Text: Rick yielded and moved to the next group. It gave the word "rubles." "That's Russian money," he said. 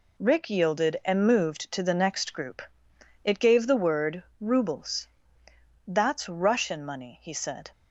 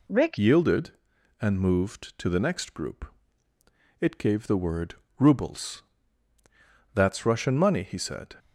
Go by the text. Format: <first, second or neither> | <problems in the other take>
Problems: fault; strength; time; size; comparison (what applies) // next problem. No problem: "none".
first | changes voice at "yielded"; from 0.3 s on; 8.0 s long // pauses between "word" and "rubles"; slight; at 4.9 s; 0.24 s long; slight in the first